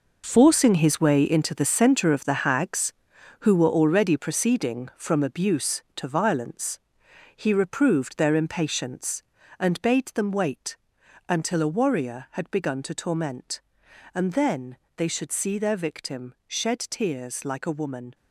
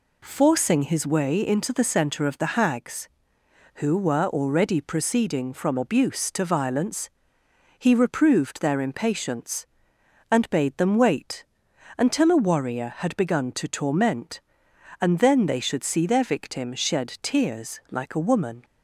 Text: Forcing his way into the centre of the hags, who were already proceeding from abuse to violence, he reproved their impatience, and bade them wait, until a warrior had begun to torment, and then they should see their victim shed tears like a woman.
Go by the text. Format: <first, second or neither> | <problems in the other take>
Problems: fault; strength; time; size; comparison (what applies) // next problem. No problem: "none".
second | gets quieter; strong; throughout; 11.5 dB // pauses between "then" and "they"; slight; at 14.7 s; 0.20 s long